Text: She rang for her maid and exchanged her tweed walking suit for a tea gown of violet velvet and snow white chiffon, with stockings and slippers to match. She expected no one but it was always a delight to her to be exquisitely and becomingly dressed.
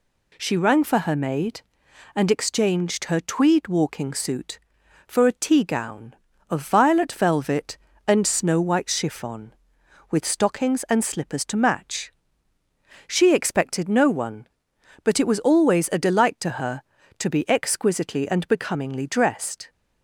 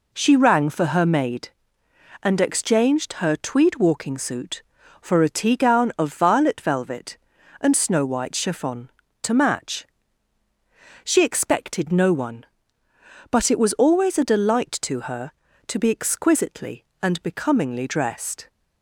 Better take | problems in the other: first | skips "with stockings and slippers"; at 9.0 s

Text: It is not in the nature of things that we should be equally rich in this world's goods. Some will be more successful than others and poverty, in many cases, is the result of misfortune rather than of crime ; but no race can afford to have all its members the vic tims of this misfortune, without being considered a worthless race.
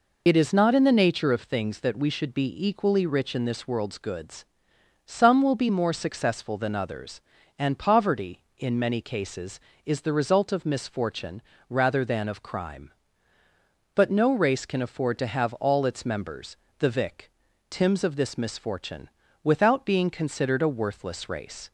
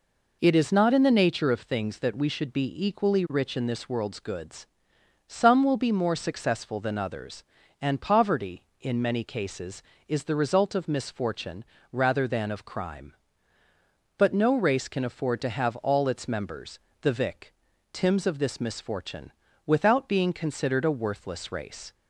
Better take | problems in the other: second | loses the start of "It"; at 0.2 s; 40 ms // pauses between "misfortune" and "rather"; slight; at 11.4 s; 0.28 s long; slight in the second // pauses between "members" and "the"; slight; at 16.5 s; 0.22 s long; slight in the second // pauses between "vic" and "tims"; at 17.3 s; 0.38 s long; also in the second

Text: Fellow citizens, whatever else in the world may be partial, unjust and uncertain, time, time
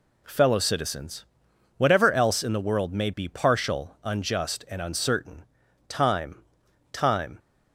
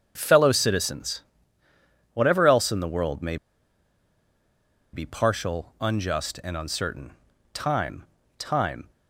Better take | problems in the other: first | starts louder than the rest; strong; until 1.1 s; 7.5 dB // pauses between "may" and "be"; strong; at 3.3 s; 1.5 s long

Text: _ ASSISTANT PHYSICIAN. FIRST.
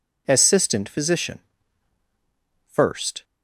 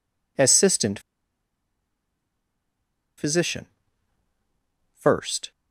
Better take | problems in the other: first | pauses between "ASSISTANT" and "PHYSICIAN"; strong; at 0.9 s; 2.1 s long

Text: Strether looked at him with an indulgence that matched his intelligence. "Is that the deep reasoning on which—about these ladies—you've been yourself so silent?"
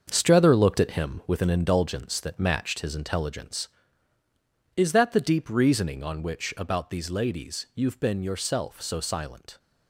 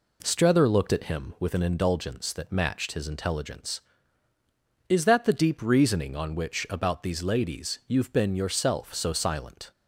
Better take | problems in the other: second | gets quieter; strong; throughout; 8.5 dB

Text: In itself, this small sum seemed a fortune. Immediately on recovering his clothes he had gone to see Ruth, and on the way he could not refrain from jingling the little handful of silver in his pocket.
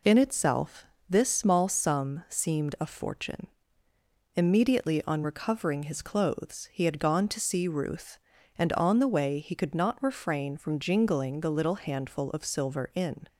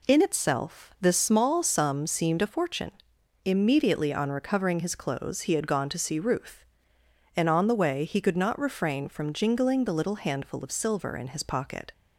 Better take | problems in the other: second | stops before "his pocket"; at 13.2 s

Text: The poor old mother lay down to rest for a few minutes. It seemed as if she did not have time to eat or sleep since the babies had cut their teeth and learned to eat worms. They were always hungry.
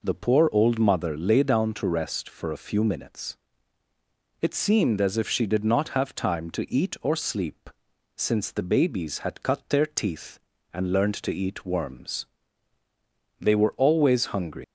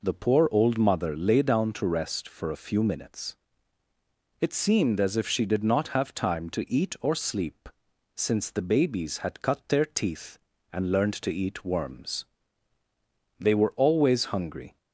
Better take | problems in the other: second | pauses between "sleep" and "since"; noticeable; at 7.6 s; 0.46 s long; noticeable in the second // leaves "hungry" unfinished; at 14.6 s; 135 ms

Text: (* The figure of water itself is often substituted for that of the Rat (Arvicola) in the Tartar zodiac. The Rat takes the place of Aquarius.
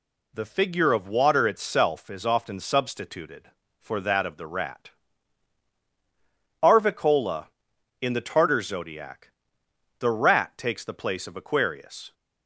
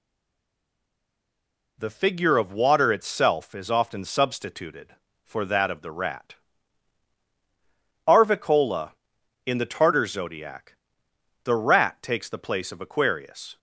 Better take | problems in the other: first | stays silent before the first word; noticeable; until 1.7 s; 1.7 s long

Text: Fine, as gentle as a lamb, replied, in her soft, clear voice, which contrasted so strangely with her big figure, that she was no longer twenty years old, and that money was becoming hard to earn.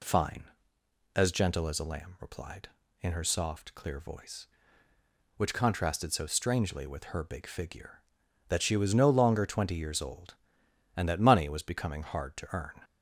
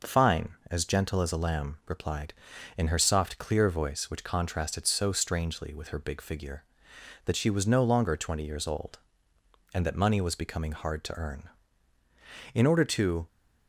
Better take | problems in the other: first | goes on to say "In order to"; noticeable; from 12.5 s on; 0.72 s long

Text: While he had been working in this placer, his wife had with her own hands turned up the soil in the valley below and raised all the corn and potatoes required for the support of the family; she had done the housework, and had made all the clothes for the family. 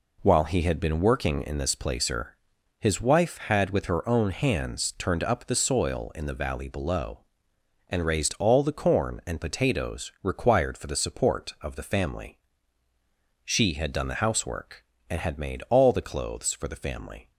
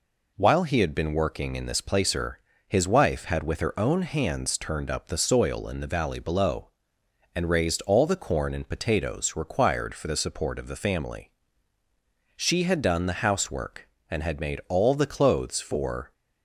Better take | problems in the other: first | stops before "the family"; at 16.1 s

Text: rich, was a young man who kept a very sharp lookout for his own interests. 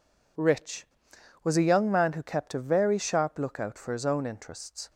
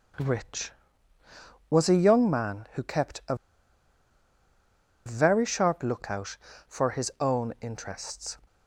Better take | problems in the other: first | pauses between "a" and "very"; strong; at 3.3 s; 1.7 s long

